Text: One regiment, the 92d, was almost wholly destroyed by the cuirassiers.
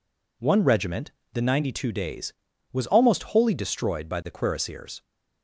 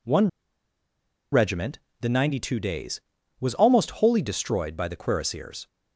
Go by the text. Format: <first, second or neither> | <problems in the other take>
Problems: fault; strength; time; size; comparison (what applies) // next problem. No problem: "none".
first | pauses between "One" and "regiment"; at 0.2 s; 1.0 s long